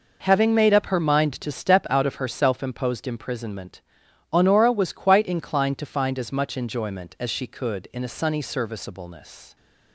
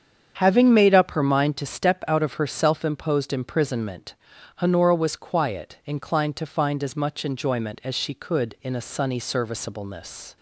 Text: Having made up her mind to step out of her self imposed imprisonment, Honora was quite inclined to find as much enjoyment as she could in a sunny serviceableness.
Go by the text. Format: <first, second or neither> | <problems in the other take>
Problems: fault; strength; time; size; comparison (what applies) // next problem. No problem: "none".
first | starts louder than the rest; strong; until 1.3 s; 7.5 dB // says "quiet" for "quite"; at 5.1 s